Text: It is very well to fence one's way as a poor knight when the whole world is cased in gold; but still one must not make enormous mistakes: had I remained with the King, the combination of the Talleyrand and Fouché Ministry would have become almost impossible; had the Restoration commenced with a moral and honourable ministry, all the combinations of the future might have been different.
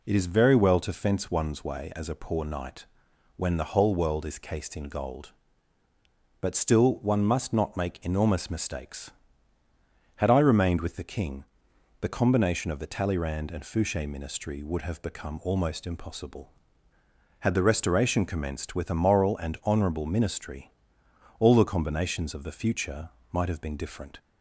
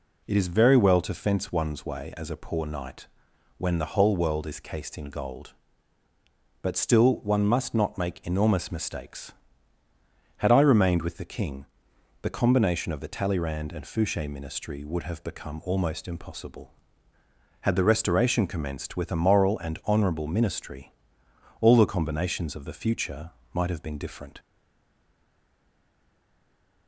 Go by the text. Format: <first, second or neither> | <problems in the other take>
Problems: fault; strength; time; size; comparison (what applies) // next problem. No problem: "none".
first | pauses between "knight" and "when"; noticeable; at 3.0 s; 0.50 s long; noticeable in the first // pauses between "future" and "might"; slight; at 23.3 s; 0.22 s long; slight in the first // stays silent after the last word; from 24.3 s on; 2.5 s long